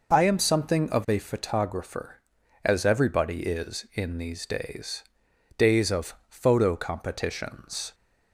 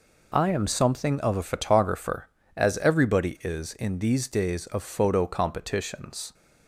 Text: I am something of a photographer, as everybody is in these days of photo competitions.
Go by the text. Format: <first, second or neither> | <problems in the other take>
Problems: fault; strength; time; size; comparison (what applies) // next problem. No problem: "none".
second | says "days" twice; at 5.5 s